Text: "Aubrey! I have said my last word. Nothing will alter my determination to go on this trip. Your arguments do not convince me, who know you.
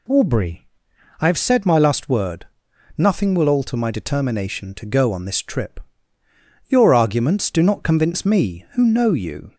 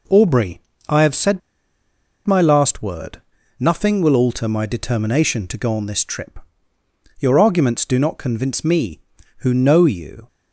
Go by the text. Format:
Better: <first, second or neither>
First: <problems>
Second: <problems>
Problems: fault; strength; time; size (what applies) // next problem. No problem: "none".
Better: first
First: none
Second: pauses between "said" and "my"; noticeable; at 1.4 s; 0.87 s long